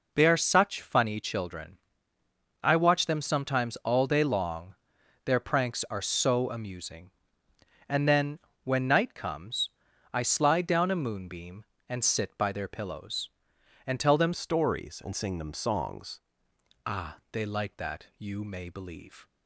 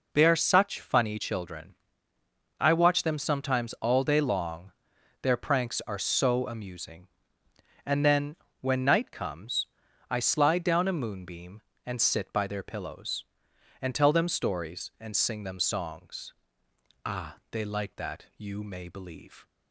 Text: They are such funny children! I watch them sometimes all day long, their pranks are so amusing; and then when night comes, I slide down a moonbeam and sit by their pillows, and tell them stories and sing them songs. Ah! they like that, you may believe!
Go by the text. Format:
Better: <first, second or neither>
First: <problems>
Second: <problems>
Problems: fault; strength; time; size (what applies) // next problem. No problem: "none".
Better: second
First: pauses between "then" and "when"; slight; at 8.3 s; 0.24 s long // changes voice from "stories" to "songs"; from 14.3 to 16.1 s; 1.8 s long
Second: pauses between "then" and "when"; slight; at 8.3 s; 0.24 s long